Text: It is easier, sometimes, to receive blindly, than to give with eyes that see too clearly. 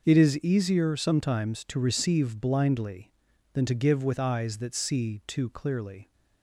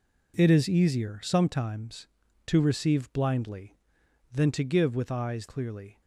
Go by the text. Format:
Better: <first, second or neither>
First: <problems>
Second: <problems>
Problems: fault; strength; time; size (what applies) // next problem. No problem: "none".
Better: first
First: none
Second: skips "that see too"; at 5.4 s